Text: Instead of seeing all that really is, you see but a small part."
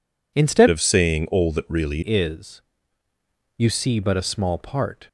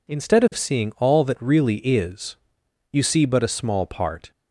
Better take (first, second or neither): second